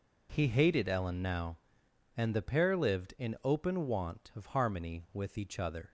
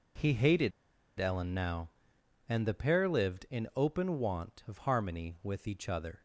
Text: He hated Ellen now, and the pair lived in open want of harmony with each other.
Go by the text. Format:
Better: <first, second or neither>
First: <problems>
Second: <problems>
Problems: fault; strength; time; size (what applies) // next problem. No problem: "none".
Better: first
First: none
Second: pauses between "hated" and "Ellen"; noticeable; at 0.7 s; 0.47 s long